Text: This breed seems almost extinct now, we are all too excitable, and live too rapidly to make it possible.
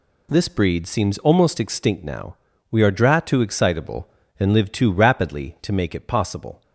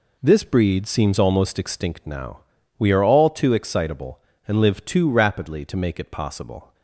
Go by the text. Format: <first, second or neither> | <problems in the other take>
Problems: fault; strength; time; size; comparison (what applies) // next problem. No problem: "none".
second | says "dra" for "all"; at 2.9 s